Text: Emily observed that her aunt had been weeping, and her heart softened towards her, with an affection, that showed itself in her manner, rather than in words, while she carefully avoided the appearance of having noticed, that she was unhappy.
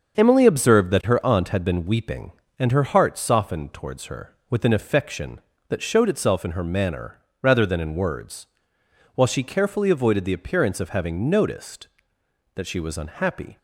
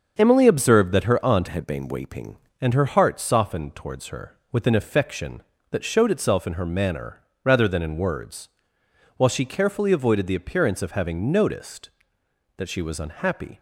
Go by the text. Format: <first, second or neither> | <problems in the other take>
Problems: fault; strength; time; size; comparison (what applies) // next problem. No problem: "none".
first | starts louder than the rest; until 1.2 s; 7 dB; also in the first // changes voice from "had" to "weeping"; from 1.4 to 2.3 s; 0.9 s long